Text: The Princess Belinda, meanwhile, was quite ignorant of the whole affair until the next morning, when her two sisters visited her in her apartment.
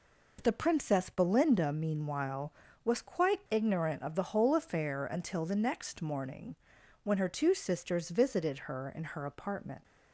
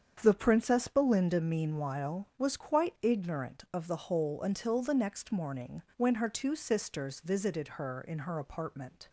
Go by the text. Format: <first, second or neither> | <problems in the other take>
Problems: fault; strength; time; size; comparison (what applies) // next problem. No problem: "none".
first | starts louder than the rest; strong; until 1.2 s; 7.5 dB // skips "affair"; at 4.4 s